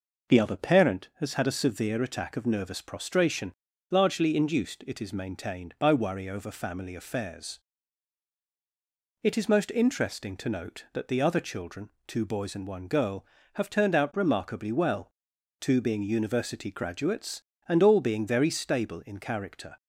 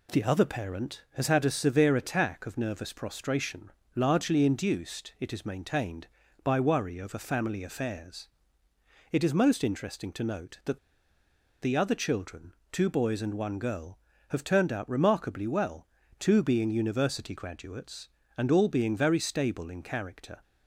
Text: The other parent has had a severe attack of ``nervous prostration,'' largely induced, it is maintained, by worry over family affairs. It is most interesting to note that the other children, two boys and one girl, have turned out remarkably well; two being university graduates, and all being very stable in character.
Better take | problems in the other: first | pauses between "that" and "the"; noticeable; at 10.7 s; 0.84 s long

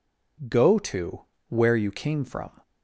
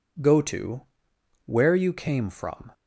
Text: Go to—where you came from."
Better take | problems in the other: neither | none

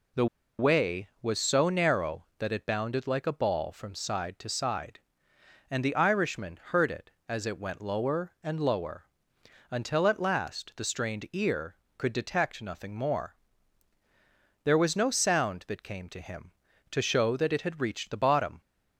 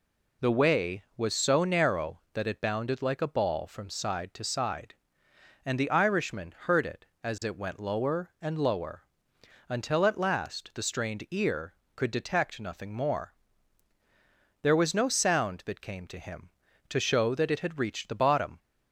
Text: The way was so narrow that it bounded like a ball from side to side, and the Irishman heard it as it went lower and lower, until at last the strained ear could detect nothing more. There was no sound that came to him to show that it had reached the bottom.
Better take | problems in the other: second | pauses between "The" and "way"; slight; at 0.2 s; 0.33 s long

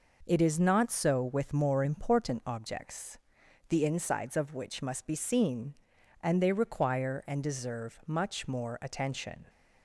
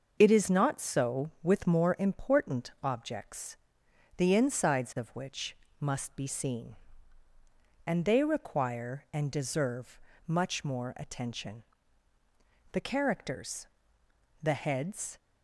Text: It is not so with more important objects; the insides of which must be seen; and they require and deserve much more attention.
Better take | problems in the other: first | starts louder than the rest; noticeable; until 1.2 s; 6 dB // pauses between "which" and "must"; slight; at 5.5 s; 0.24 s long // pauses between "deserve" and "much"; slight; at 9.9 s; 0.28 s long // goes on to say "The characters the heads"; strong; from 12.7 s on; 2.4 s long

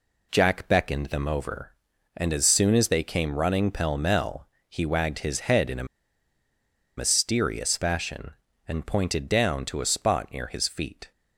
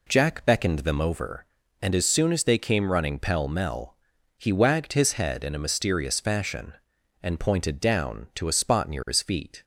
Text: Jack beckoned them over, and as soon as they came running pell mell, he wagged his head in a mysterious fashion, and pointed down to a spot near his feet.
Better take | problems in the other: second | pauses between "a" and "mysterious"; at 5.8 s; 1.1 s long

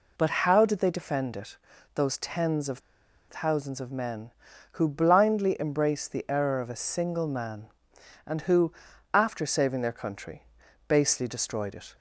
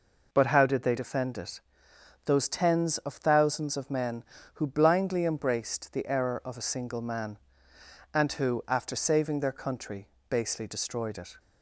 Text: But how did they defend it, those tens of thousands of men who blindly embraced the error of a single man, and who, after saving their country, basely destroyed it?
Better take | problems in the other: second | pauses between "of" and "thousands"; noticeable; at 2.7 s; 0.50 s long

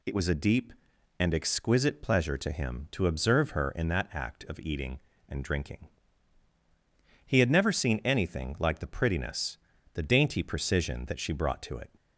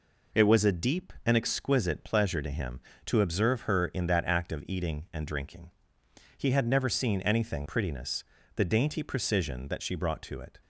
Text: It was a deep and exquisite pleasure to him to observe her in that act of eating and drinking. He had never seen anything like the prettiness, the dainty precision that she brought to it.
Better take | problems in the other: first | skips "like the"; at 7.6 s

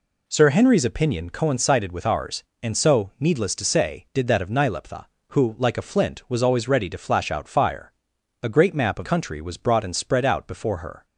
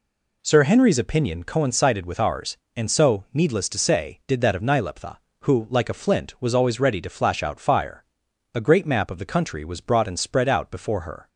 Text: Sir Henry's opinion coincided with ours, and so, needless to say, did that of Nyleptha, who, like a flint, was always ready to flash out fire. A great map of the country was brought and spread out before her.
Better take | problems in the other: second | skips "the"; at 9.0 s

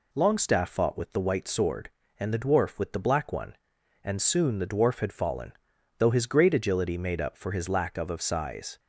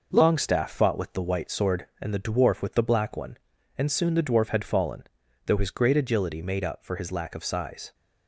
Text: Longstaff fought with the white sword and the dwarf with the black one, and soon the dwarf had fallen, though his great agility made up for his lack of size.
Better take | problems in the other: second | says "of" twice; at 8.1 s

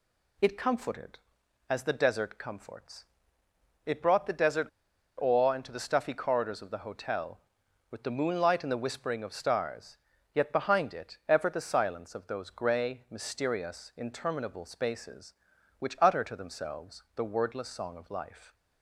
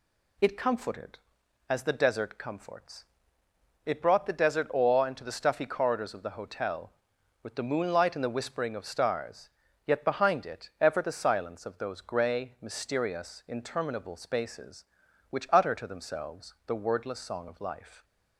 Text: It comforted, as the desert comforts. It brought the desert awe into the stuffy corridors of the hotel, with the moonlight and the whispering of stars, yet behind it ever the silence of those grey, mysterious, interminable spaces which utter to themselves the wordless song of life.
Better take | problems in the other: second | pauses between "desert" and "awe"; noticeable; at 4.6 s; 0.51 s long

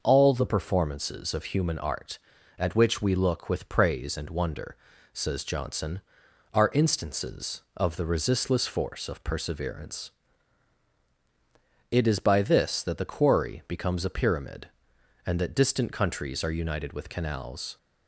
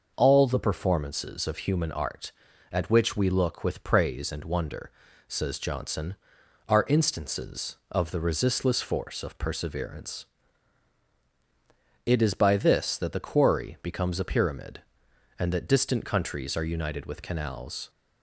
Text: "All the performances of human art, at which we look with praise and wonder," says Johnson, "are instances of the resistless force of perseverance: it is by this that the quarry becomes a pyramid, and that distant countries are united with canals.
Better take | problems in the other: neither | none

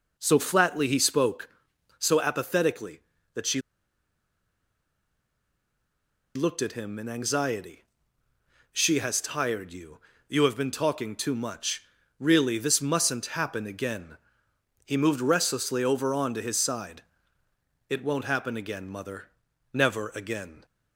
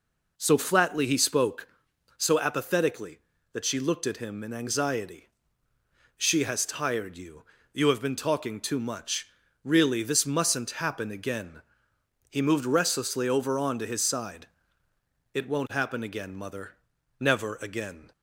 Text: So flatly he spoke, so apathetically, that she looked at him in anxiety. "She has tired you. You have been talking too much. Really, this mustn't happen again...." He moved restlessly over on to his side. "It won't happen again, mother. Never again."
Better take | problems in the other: second | pauses between "she" and "looked"; strong; at 3.6 s; 2.7 s long

